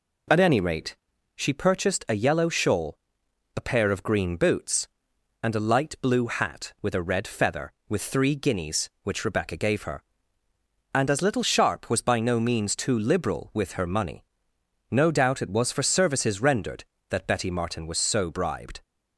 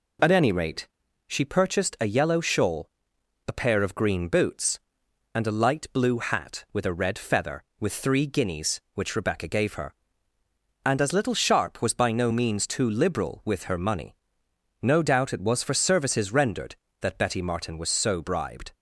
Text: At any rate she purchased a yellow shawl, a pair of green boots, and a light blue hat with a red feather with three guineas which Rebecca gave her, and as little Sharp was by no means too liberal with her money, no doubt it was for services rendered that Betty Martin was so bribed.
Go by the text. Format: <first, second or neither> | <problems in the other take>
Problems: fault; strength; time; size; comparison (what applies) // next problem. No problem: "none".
neither | pauses between "rate" and "she"; the same in both